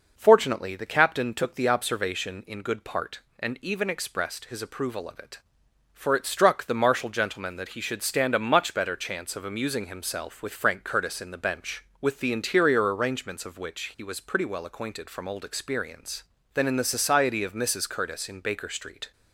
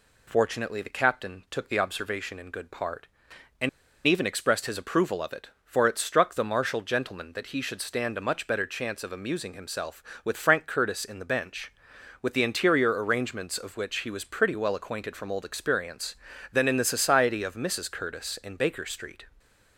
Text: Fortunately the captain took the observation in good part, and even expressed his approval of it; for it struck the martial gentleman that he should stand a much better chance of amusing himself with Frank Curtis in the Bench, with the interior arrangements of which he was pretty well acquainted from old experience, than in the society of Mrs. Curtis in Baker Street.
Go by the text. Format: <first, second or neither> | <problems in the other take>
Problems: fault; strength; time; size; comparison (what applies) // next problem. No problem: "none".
first | pauses between "and" and "even"; at 3.6 s; 0.38 s long